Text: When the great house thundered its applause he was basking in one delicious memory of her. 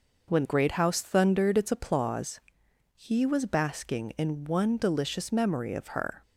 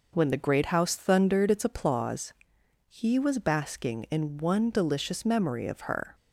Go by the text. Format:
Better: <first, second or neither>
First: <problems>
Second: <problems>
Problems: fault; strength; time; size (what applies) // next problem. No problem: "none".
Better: second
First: skips "the"; at 0.4 s // pauses between "applause" and "he"; noticeable; at 2.3 s; 0.54 s long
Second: pauses between "applause" and "he"; noticeable; at 2.3 s; 0.54 s long